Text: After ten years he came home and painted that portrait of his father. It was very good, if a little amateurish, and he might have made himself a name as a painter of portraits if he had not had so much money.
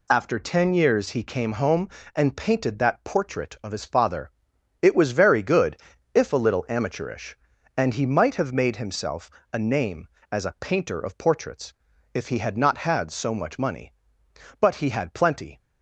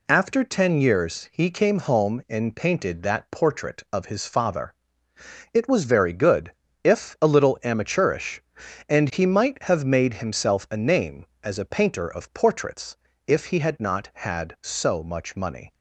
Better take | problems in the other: second | pauses between "himself" and "a"; slight; at 9.3 s; 0.22 s long // pauses between "portraits" and "if"; at 11.7 s; 0.42 s long; slight in the second // goes on to say "But he had plenty"; noticeable; from 14.6 s on; 0.98 s long

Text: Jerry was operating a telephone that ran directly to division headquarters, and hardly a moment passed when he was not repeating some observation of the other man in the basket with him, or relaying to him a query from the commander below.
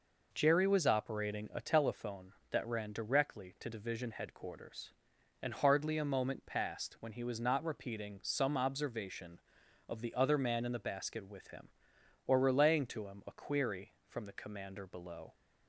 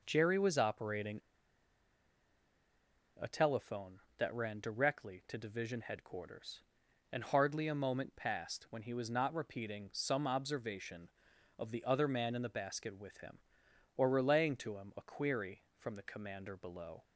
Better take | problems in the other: first | pauses between "operating" and "a"; strong; at 1.1 s; 1.9 s long

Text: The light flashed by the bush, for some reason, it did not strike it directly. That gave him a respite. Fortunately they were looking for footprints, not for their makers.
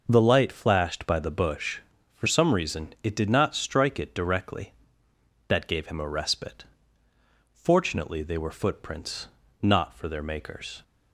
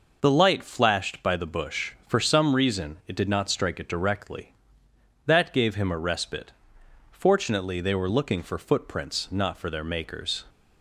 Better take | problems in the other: second | skips "looking for"; at 8.5 s

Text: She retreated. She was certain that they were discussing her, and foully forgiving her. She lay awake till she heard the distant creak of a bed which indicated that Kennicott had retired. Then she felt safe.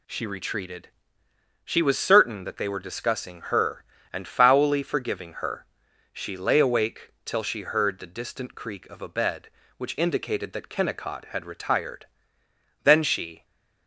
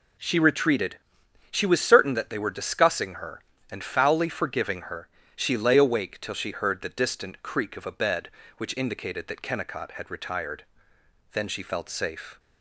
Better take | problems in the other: second | pauses between "awake" and "till"; slight; at 7.0 s; 0.16 s long // stops before "felt safe"; at 13.4 s

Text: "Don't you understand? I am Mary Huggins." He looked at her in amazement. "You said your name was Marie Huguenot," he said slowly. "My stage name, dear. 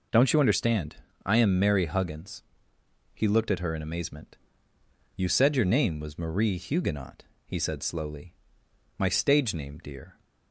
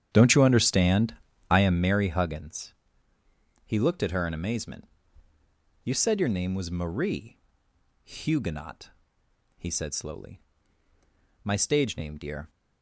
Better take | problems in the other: first | starts louder than the rest; strong; until 1.9 s; 9 dB // pauses between "Marie" and "Huguenot"; noticeable; at 7.3 s; 0.64 s long

